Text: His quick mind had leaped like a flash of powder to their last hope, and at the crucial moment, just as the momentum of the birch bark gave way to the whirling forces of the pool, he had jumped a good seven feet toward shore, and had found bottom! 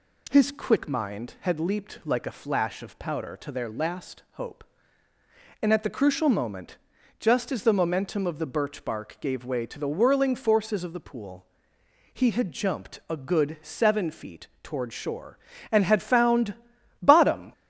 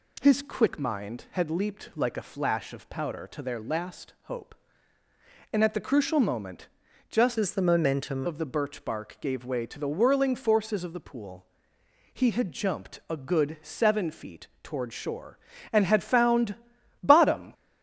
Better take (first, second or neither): first